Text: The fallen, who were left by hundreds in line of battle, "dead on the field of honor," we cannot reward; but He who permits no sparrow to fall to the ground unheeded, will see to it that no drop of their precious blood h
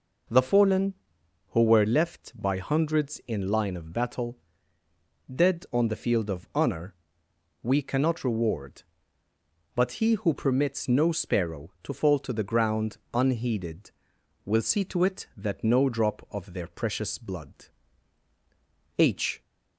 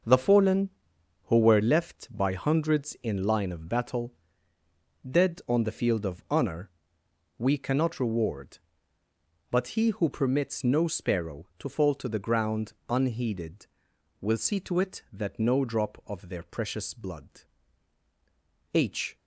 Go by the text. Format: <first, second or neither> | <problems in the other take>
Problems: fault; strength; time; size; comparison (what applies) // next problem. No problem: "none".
first | gets quieter; strong; throughout; 9.5 dB // pauses between "ground" and "unheeded"; slight; at 12.7 s; 0.16 s long; slight in the first // pauses between "blood" and "h"; strong; at 17.4 s; 1.3 s long; strong in the first